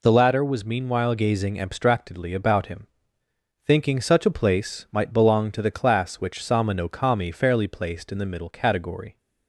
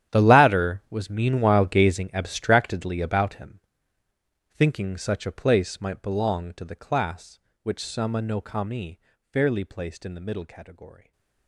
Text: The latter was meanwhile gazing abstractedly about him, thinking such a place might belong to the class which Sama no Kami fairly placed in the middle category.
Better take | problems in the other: first | gets quieter; strong; throughout; 17.5 dB // pauses between "Kami" and "fairly"; slight; at 8.9 s; 0.34 s long // stays silent after the last word; slight; from 10.9 s on; 0.5 s long

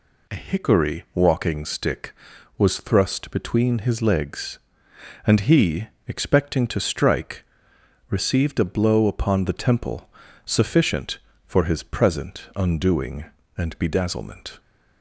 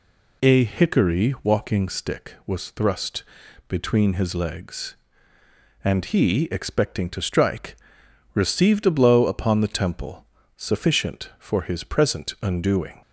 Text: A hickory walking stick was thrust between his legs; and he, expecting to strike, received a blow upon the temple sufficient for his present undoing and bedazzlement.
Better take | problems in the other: first | pauses between "thrust" and "between"; noticeable; at 3.2 s; 0.46 s long // pauses between "temple" and "sufficient"; slight; at 10.2 s; 0.28 s long; slight in the first // stops before "and bedazzlement"; at 13.0 s

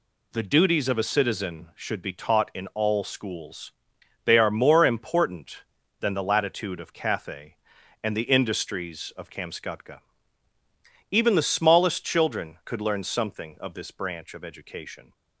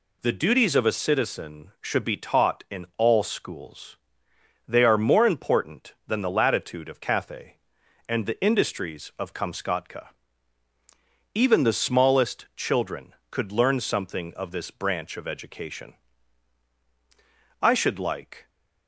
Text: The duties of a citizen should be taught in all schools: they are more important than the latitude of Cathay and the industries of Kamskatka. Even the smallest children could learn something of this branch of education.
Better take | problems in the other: first | goes on to say "I should like"; noticeable; from 17.6 s on; 0.88 s long

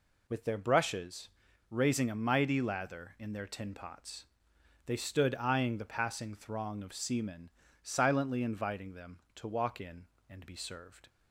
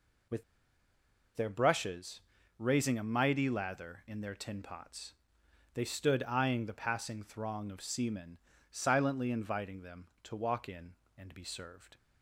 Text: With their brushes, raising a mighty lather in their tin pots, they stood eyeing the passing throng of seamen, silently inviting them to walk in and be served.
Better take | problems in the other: first | pauses between "With" and "their"; noticeable; at 0.4 s; 0.93 s long

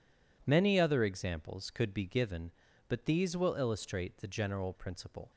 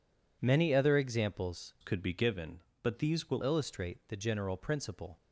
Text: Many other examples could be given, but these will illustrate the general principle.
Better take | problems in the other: first | changes voice from "could" to "will"; from 1.8 to 3.4 s; 1.6 s long

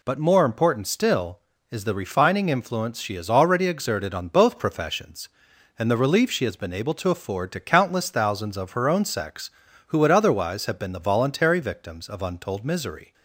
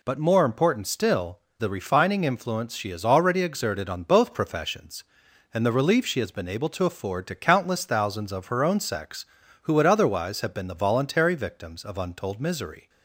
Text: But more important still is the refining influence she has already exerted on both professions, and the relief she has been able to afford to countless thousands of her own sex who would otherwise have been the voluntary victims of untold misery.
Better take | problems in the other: first | skips "is"; at 1.4 s

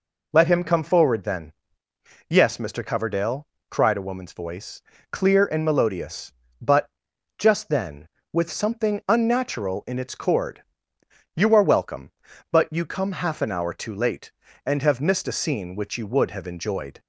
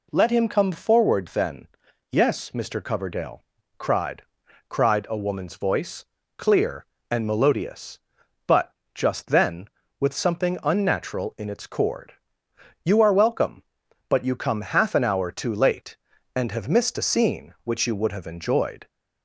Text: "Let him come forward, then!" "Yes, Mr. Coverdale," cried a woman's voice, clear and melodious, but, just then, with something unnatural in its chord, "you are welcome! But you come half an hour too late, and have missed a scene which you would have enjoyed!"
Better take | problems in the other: first | says "cried" twice; at 4.7 s

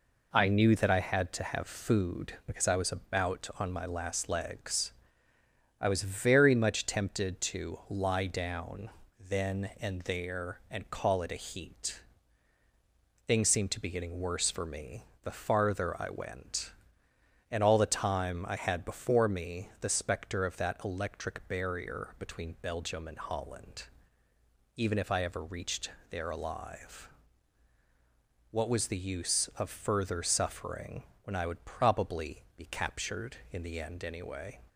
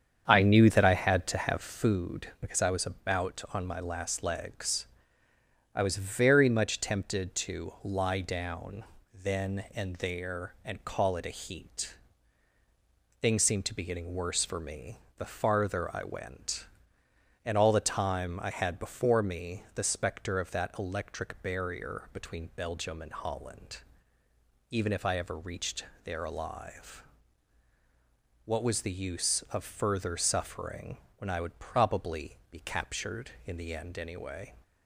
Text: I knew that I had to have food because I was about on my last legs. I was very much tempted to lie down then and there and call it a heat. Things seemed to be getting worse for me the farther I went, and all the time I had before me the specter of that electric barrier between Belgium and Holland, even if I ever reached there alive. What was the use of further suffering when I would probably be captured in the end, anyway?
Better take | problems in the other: first | starts louder than the rest; strong; until 1.7 s; 8 dB // pauses between "down" and "then"; slight; at 8.8 s; 0.32 s long; slight in the first // pauses between "me" and "the"; slight; at 14.9 s; 0.20 s long; slight in the first // pauses between "reached" and "there"; slight; at 25.8 s; 0.20 s long; slight in the first // pauses between "suffering" and "when"; slight; at 30.9 s; 0.18 s long; slight in the first // pauses between "probably" and "be"; slight; at 32.3 s; 0.16 s long; slight in the first

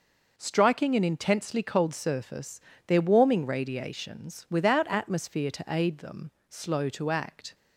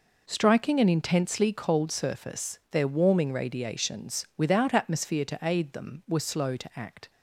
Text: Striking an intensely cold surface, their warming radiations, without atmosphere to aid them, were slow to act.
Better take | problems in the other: second | skips "were"; at 6.3 s

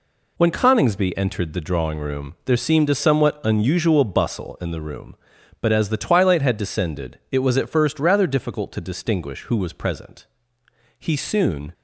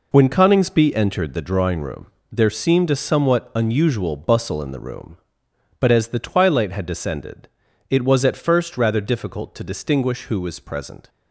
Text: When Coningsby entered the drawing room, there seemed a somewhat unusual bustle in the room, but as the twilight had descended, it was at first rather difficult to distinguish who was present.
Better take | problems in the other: second | goes on to say "He soon"; noticeable; from 10.9 s on; 0.74 s long

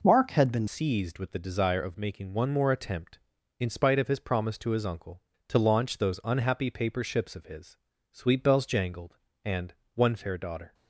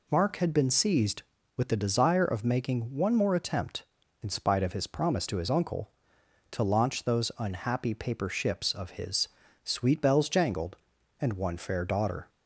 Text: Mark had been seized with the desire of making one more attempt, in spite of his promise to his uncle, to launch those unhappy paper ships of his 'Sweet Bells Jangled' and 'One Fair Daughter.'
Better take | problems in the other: second | changes voice at "seized"; from 0.6 s on; 10.1 s long // pauses between "his" and "Sweet"; slight; at 7.7 s; 0.36 s long; also in the second // pauses between "and" and "One"; slight; at 9.7 s; 0.20 s long

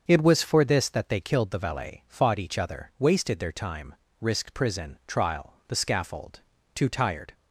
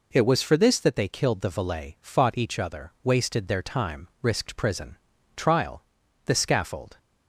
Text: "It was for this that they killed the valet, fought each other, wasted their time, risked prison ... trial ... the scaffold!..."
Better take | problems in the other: second | starts louder than the rest; until 1.1 s; 6.5 dB // goes on to say "Too tired"; from 6.7 s on; 0.58 s long

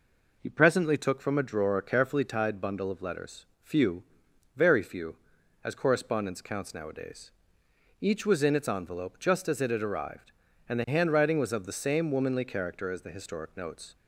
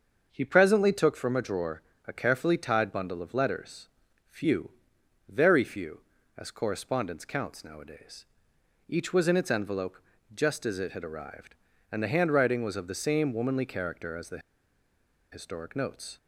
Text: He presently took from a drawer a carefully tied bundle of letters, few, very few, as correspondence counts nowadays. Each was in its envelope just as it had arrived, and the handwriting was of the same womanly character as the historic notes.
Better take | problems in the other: first | starts louder than the rest; until 1.3 s; 6.5 dB // pauses between "drawer" and "a"; slight; at 1.8 s; 0.24 s long // pauses between "envelope" and "just"; slight; at 9.9 s; 0.36 s long // pauses between "the" and "historic"; noticeable; at 14.3 s; 0.93 s long

